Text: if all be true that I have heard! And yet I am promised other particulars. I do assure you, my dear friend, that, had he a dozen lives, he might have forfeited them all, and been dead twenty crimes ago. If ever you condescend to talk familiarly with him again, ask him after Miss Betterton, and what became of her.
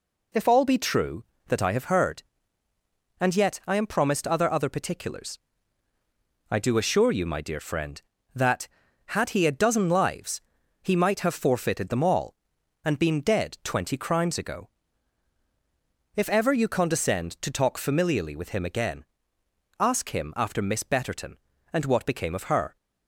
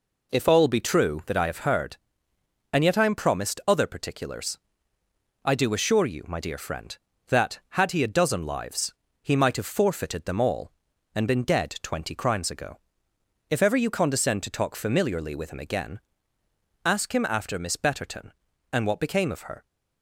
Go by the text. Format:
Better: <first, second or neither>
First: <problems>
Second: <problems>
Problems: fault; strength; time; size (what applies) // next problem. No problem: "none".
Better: second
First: says "other" twice; at 4.5 s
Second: none